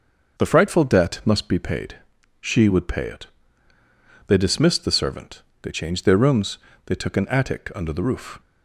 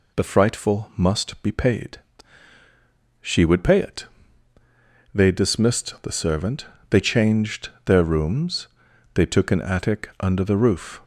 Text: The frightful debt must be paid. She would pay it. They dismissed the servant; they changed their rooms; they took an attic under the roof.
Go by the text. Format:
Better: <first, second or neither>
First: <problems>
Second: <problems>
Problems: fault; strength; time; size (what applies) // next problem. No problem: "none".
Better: first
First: none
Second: skips "debt"; at 0.9 s // pauses between "changed" and "their"; slight; at 7.6 s; 0.16 s long